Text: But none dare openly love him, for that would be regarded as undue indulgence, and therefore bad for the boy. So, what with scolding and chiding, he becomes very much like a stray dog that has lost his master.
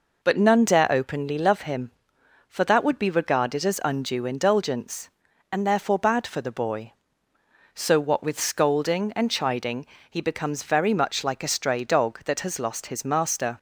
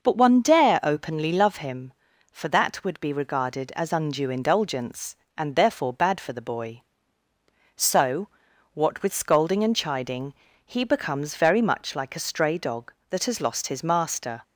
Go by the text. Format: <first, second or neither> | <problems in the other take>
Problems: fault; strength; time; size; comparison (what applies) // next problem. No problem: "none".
first | says "one" for "none"; at 0.1 s